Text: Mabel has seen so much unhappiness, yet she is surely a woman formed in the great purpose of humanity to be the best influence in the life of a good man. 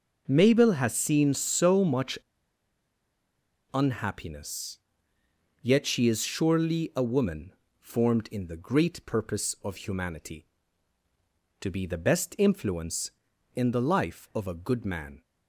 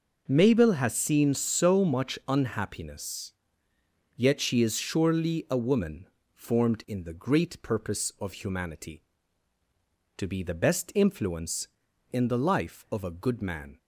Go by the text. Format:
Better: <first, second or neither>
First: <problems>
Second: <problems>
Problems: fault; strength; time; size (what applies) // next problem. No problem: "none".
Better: second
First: pauses between "much" and "unhappiness"; strong; at 2.1 s; 1.5 s long // pauses between "woman" and "formed"; slight; at 7.5 s; 0.26 s long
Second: pauses between "woman" and "formed"; slight; at 6.0 s; 0.26 s long